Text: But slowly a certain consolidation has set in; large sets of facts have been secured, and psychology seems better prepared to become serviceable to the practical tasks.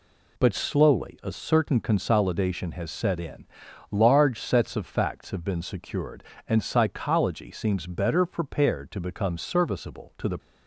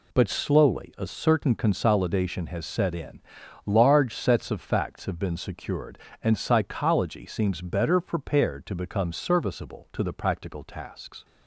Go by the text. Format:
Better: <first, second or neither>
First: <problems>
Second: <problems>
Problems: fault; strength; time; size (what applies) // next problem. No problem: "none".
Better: second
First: stops before "practical tasks"; at 10.3 s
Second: none